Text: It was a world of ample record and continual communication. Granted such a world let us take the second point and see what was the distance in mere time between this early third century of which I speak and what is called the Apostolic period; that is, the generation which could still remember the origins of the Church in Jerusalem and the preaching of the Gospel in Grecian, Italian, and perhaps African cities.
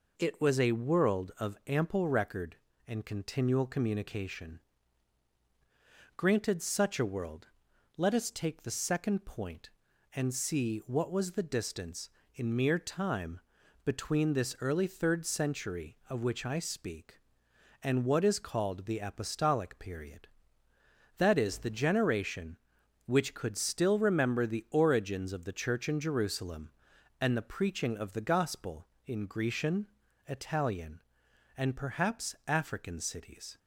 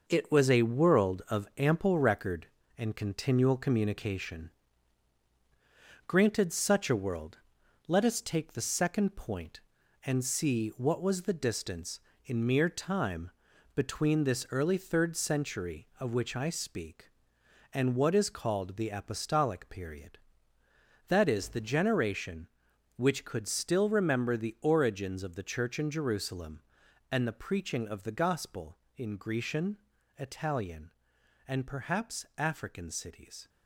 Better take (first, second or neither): first